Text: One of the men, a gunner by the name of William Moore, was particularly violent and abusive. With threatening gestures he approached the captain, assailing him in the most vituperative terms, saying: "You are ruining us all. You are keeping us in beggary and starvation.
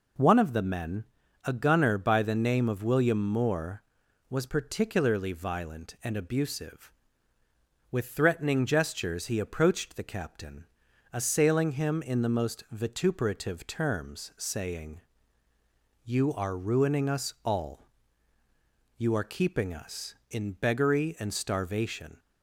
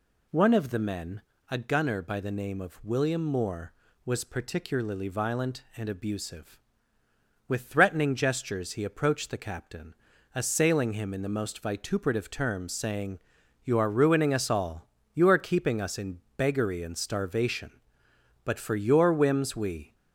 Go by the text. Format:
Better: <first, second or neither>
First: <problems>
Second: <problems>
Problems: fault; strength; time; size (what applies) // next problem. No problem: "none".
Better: first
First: none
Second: pauses between "in" and "beggary"; slight; at 16.2 s; 0.16 s long // goes on to say "But for your whims we"; from 18.4 s on; 1.5 s long